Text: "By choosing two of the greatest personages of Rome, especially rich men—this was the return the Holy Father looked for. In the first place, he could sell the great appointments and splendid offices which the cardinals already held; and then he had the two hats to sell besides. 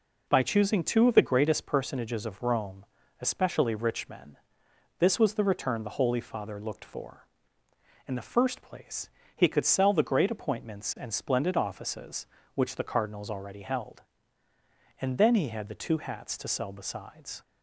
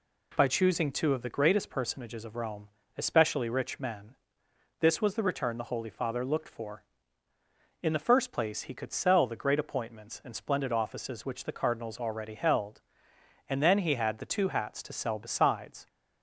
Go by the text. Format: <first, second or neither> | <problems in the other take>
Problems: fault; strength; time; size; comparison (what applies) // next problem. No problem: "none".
neither | none